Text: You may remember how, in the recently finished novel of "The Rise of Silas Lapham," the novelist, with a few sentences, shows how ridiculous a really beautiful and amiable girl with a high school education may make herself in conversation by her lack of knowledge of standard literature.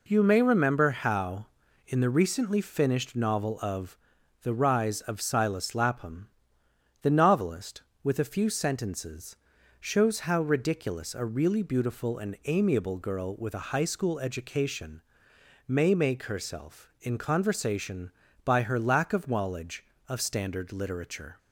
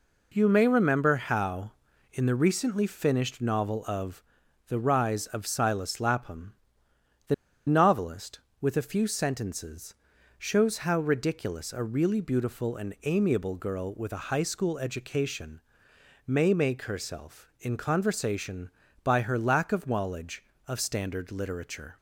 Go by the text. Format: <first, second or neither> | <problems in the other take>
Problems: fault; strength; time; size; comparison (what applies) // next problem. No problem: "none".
first | pauses between "of" and "The"; noticeable; at 4.2 s; 0.46 s long; noticeable in the first // pauses between "the" and "novelist"; slight; at 7.3 s; 0.34 s long // pauses between "education" and "may"; noticeable; at 15.6 s; 0.66 s long; noticeable in the first